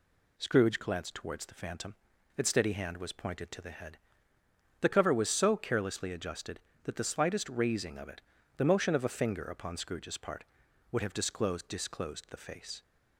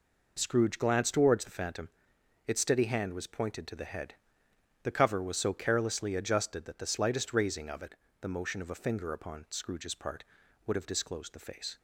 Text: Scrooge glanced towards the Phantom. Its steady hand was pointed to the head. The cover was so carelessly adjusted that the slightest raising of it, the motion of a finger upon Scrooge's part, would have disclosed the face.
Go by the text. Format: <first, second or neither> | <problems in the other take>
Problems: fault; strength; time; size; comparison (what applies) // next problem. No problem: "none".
second | says "disclosed" twice; at 11.6 s